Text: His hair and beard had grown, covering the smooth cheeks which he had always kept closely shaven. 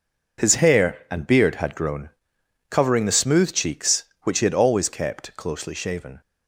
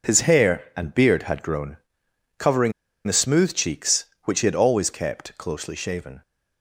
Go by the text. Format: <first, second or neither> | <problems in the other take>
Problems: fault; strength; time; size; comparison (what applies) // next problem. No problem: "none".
first | pauses between "covering" and "the"; slight; at 2.7 s; 0.35 s long